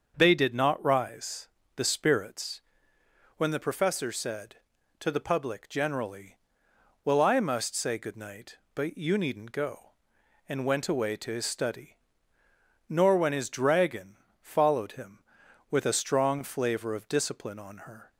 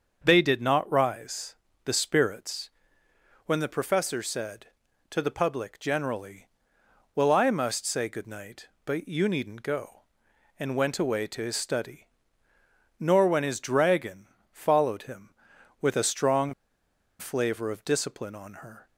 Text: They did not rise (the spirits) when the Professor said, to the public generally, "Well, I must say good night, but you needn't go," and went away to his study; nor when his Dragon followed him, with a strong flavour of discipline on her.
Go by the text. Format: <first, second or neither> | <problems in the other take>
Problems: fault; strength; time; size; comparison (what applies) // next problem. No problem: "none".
first | starts louder than the rest; until 1.2 s; 6.5 dB; also in the first // pauses between "Dragon" and "followed"; slight; at 14.2 s; 0.24 s long; slight in the first // pauses between "strong" and "flavour"; noticeable; at 16.5 s; 0.66 s long